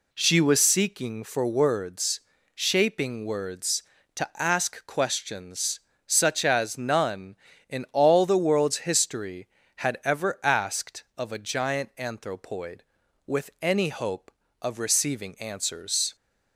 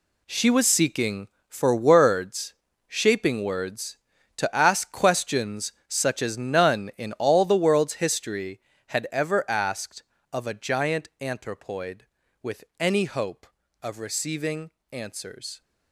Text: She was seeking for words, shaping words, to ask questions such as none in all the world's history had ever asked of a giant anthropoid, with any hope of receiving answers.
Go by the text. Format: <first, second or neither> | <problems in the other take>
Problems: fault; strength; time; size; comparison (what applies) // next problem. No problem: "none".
first | gets quieter; strong; throughout; 11 dB // pauses between "questions" and "such"; slight; at 5.7 s; 0.16 s long; slight in the first // pauses between "with" and "any"; slight; at 12.6 s; 0.16 s long // pauses between "receiving" and "answers"; slight; at 14.7 s; 0.20 s long